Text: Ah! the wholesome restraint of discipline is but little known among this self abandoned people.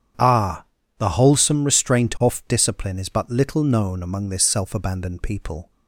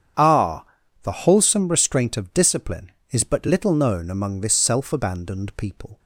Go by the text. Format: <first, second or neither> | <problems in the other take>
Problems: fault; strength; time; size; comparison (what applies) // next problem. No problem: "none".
second | starts louder than the rest; strong; until 1.5 s; 8.5 dB; strong in the second // says "off" for "of"; at 2.2 s